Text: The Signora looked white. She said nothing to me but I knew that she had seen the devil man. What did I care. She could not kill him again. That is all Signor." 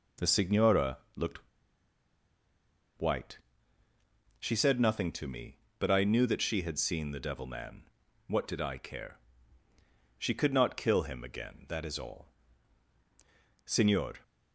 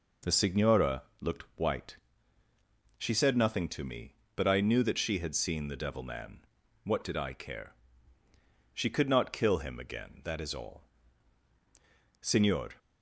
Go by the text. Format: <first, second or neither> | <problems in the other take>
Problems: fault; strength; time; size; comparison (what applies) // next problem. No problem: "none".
second | pauses between "Signora" and "looked"; slight; at 0.9 s; 0.18 s long; slight in the second // pauses between "looked" and "white"; strong; at 1.3 s; 1.6 s long // pauses between "all" and "Signor"; strong; at 12.2 s; 1.3 s long; strong in the second